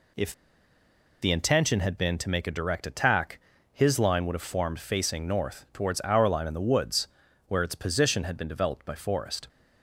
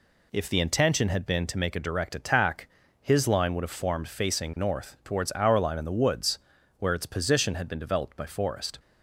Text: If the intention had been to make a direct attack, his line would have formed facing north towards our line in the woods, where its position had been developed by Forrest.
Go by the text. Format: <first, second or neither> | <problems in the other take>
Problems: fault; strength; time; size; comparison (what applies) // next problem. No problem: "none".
second | pauses between "If" and "the"; noticeable; at 0.3 s; 0.90 s long